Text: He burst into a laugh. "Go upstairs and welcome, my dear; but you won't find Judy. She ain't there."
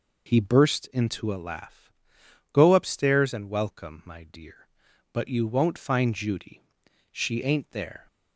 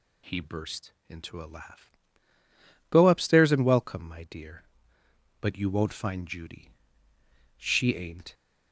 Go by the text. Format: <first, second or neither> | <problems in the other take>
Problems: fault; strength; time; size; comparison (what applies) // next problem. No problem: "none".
first | pauses between "burst" and "into"; slight; at 0.9 s; 0.16 s long // stops before "there"; at 8.3 s